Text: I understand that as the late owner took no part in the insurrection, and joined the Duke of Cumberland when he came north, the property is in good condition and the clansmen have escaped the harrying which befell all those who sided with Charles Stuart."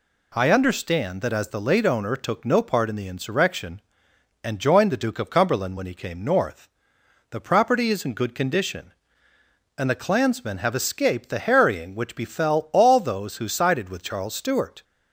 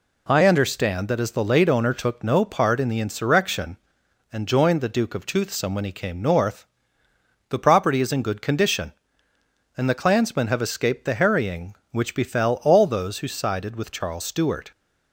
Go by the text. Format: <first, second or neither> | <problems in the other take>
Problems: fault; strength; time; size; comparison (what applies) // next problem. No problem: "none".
first | says "Toothsome" for "Cumberland"; at 5.2 s